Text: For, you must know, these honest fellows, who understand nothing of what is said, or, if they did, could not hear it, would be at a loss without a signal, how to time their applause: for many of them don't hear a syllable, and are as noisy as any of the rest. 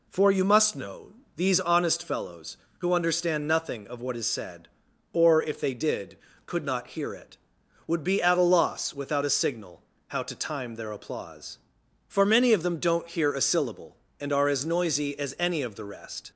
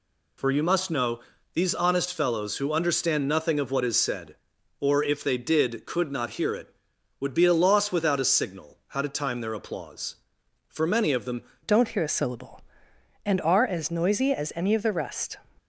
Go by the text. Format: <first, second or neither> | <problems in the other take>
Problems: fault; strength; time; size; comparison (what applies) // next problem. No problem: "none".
first | changes voice at "don't"; from 11.6 s on; 3.7 s long